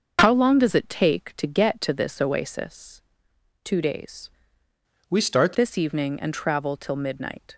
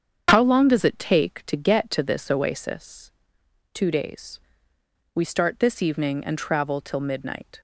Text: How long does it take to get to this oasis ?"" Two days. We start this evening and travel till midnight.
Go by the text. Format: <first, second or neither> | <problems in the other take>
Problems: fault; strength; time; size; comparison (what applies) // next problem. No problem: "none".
second | starts louder than the rest; until 1.2 s; 6.5 dB; strong in the second // changes voice from "We" to "start"; from 5.0 to 5.5 s; 0.5 s long